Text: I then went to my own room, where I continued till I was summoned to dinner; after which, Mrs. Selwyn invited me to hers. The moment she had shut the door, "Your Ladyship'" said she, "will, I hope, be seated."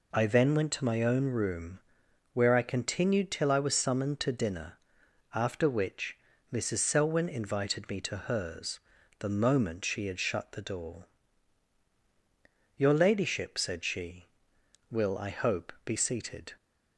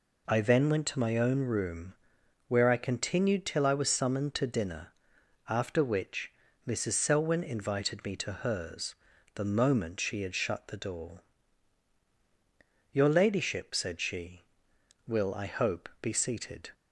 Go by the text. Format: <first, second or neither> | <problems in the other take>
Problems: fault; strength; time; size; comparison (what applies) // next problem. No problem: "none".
neither | none